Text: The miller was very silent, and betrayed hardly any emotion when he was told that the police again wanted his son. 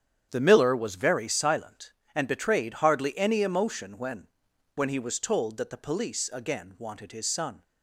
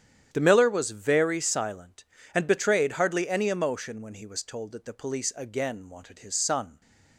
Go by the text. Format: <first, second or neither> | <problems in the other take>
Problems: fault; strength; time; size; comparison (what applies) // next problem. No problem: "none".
second | starts louder than the rest; strong; until 1.3 s; 8.5 dB; strong in the second // says "when" twice; at 4.7 s